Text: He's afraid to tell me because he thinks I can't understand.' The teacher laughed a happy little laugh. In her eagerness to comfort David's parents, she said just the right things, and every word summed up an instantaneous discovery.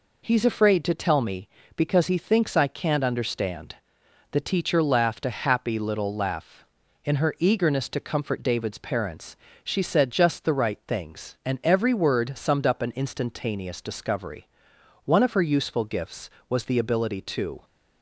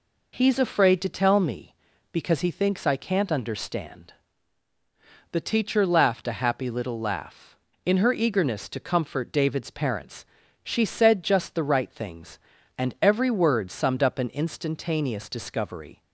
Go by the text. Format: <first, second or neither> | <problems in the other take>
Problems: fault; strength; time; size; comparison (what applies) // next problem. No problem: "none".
second | goes on to say "One of her useful gifts was the ability to"; strong; from 15.0 s on; 2.6 s long